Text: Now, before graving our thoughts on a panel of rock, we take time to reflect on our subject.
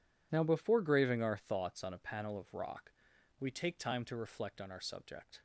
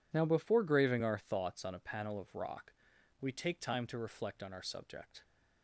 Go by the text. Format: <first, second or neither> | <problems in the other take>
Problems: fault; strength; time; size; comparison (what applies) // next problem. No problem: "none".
neither | none